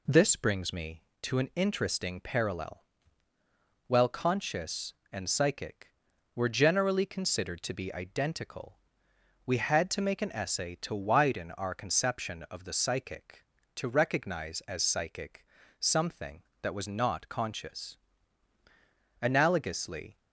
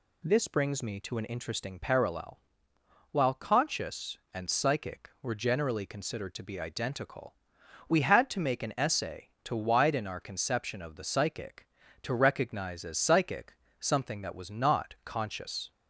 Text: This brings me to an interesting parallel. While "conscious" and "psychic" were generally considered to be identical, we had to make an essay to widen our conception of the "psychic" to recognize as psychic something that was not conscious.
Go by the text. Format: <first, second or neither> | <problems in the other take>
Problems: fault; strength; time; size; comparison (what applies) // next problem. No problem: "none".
second | pauses between "psychic" and "something"; slight; at 15.4 s; 0.36 s long; slight in the second // goes on to say "Analogously"; noticeable; from 19.2 s on; 0.98 s long